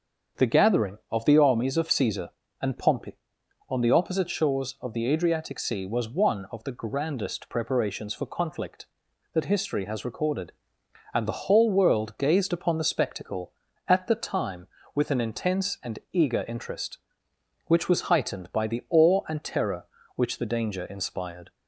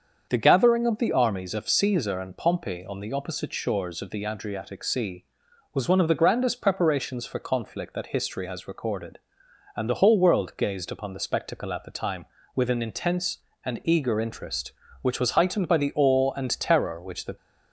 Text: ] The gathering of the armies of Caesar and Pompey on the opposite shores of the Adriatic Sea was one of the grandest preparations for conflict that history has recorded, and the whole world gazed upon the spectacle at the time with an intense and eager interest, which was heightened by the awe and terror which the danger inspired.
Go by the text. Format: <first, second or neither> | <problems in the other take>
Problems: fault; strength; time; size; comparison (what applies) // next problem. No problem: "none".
first | starts louder than the rest; until 1.3 s; 7 dB; also in the first // stops before "danger inspired"; at 17.3 s